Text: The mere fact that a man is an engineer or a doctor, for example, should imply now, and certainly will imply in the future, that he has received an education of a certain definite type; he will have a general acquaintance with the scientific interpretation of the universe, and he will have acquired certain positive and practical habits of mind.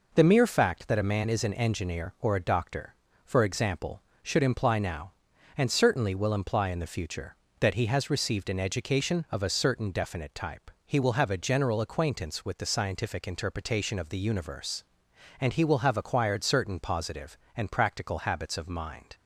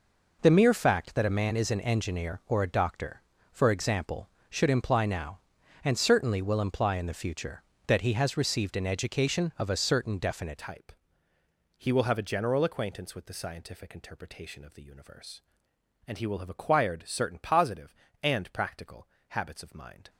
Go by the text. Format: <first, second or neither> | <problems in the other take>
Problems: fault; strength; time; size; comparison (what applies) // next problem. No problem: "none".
first | changes voice at "type"; from 10.5 s on; 9.5 s long // pauses between "practical" and "habits"; slight; at 19.0 s; 0.22 s long